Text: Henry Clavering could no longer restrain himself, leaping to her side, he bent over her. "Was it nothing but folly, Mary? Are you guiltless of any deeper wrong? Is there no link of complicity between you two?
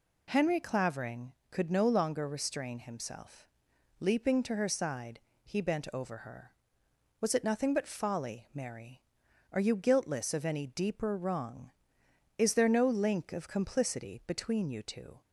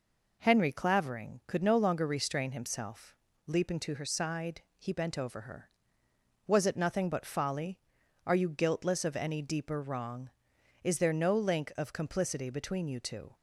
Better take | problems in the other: first | skips "Mary"; at 8.0 s

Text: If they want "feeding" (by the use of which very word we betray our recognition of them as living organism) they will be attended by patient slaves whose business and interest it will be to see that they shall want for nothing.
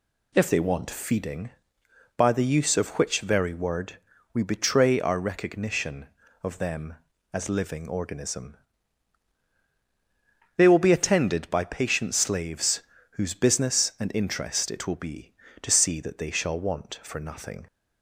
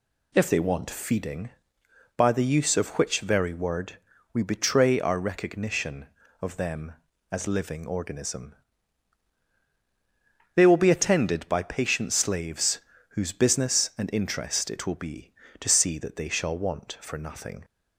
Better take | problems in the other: neither | pauses between "word" and "we"; slight; the same in both // pauses between "slaves" and "whose"; slight; the same in both

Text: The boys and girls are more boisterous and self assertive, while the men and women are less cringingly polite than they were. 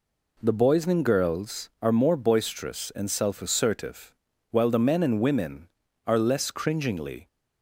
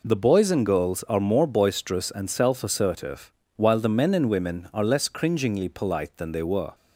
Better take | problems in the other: second | stops before "polite than they were"; at 7.2 s

